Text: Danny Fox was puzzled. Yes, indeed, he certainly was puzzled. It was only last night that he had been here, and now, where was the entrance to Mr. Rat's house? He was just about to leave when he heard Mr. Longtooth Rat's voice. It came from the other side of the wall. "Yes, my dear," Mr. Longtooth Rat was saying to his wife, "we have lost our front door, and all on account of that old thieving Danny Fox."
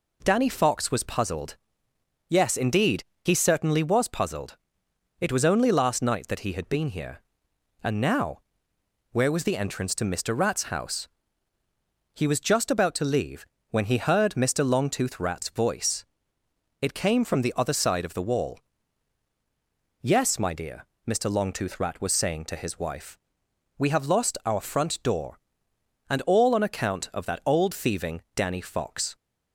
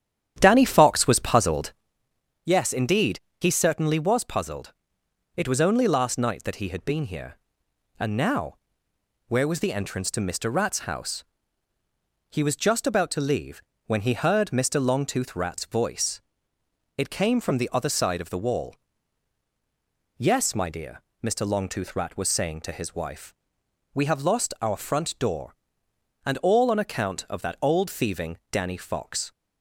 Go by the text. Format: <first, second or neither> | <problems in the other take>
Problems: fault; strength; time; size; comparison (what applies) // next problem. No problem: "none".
first | starts louder than the rest; strong; until 1.9 s; 10 dB // pauses between "leave" and "when"; slight; at 13.6 s; 0.26 s long; slight in the first